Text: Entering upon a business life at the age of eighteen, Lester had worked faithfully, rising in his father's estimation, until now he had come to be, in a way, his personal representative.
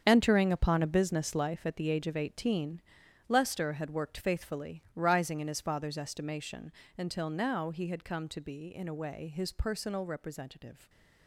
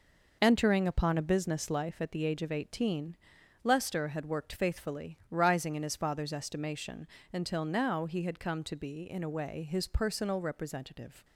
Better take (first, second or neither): second